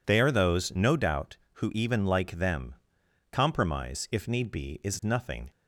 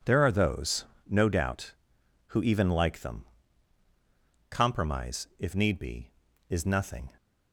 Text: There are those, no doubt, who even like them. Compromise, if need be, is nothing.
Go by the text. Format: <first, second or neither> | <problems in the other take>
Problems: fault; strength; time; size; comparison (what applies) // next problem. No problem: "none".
second | says "They" for "There"; at 0.0 s